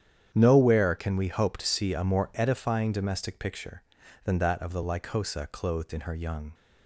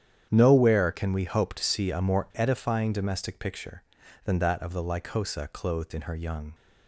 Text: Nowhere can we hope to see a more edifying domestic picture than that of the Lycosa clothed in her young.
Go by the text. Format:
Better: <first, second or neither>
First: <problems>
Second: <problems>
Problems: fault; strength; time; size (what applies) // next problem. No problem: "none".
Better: neither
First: starts louder than the rest; strong; until 1.3 s; 9 dB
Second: starts louder than the rest; strong; until 1.3 s; 9 dB